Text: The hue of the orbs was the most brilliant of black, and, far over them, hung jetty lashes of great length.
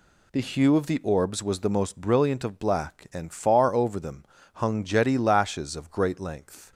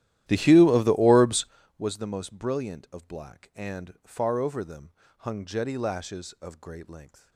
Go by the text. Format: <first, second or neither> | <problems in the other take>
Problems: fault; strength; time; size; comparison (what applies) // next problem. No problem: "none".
first | starts louder than the rest; strong; until 1.6 s; 13 dB